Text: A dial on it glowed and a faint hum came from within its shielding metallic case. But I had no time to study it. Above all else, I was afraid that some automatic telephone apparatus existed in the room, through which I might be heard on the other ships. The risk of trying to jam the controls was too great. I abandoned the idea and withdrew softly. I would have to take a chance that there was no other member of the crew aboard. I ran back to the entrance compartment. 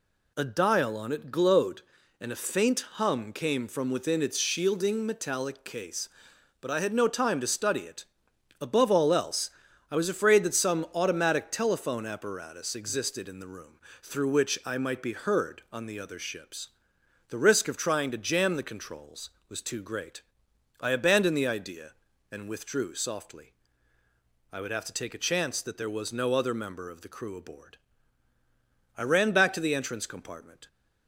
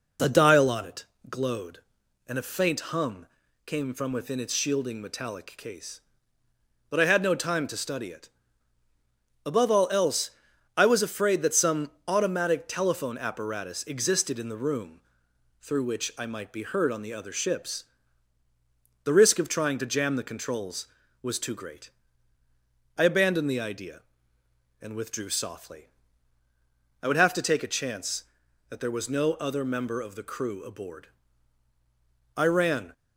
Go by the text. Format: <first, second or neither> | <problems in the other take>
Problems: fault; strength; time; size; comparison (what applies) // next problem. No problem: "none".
first | pauses between "it" and "glowed"; slight; at 1.0 s; 0.24 s long // pauses between "hum" and "came"; at 3.2 s; 0.40 s long // pauses between "some" and "automatic"; slight; at 11.8 s; 0.18 s long // stops before "back to the entrance compartment"; at 32.9 s